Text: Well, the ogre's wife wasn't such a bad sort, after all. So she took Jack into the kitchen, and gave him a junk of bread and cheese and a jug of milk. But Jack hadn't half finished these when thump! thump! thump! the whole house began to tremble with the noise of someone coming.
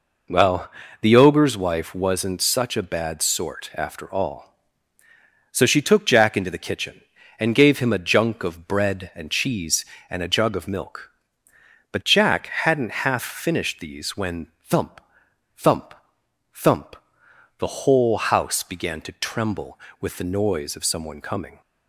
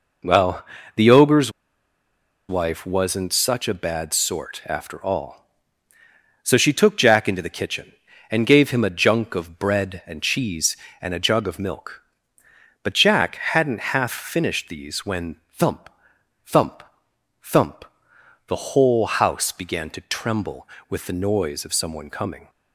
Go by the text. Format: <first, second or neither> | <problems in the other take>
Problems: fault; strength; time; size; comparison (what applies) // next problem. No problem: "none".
first | pauses between "ogre's" and "wife"; at 1.5 s; 0.98 s long